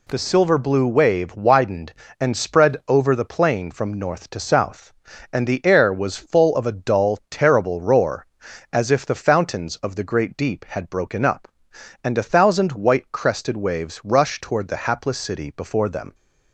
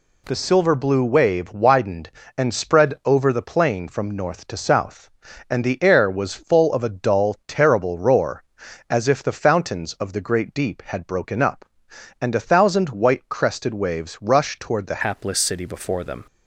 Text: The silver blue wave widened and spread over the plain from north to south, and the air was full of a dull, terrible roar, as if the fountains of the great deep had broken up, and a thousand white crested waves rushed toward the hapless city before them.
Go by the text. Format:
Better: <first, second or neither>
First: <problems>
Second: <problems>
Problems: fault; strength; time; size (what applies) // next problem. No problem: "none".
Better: first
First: none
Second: changes voice at "hapless"; from 15.0 s on; 1.2 s long